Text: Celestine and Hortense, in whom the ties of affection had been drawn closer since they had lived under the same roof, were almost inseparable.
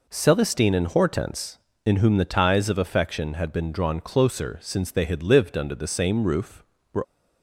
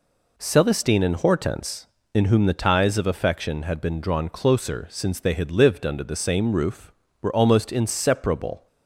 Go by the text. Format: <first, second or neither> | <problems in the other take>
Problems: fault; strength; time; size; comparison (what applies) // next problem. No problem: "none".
second | stops before "almost inseparable"; at 7.0 s